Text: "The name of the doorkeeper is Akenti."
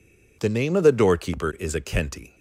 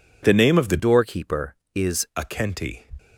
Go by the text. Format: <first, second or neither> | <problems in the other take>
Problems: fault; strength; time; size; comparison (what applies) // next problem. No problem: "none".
first | changes voice from "doorkeeper" to "is"; from 0.7 to 2.0 s; 1.3 s long